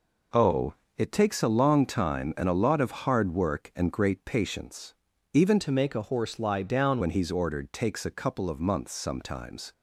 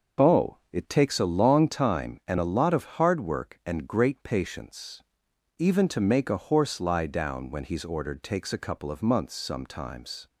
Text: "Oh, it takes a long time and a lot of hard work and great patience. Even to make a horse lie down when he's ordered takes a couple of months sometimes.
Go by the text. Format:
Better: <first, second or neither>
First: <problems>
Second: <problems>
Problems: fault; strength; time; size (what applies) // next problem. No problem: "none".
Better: second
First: changes voice from "to" to "down"; from 5.5 to 7.0 s; 1.5 s long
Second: none